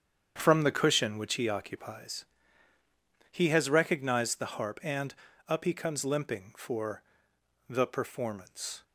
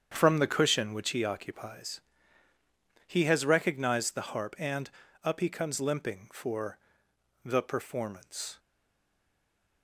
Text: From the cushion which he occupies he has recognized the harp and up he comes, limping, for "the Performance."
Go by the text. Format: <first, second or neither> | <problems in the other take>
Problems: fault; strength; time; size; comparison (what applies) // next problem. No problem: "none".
first | starts louder than the rest; strong; until 1.1 s; 8 dB; strong in the first // pauses between "occupies" and "he"; at 2.0 s; 1.0 s long; also in the first // pauses between "and" and "up"; slight; at 4.8 s; 0.36 s long; slight in the first // pauses between "for" and "the"; noticeable; at 6.7 s; 0.64 s long; noticeable in the first // stays silent after the last word; noticeable; from 8.5 s on; 1.3 s long